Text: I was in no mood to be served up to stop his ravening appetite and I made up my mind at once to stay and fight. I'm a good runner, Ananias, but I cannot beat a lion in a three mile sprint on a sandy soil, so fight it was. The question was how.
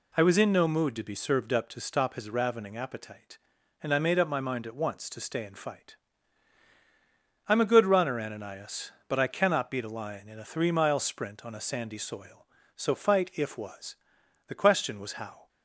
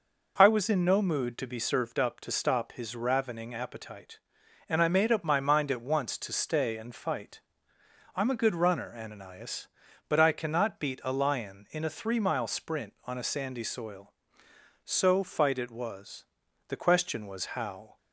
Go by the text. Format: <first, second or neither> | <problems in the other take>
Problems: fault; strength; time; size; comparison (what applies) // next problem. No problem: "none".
second | says "if" for "it"; at 13.3 s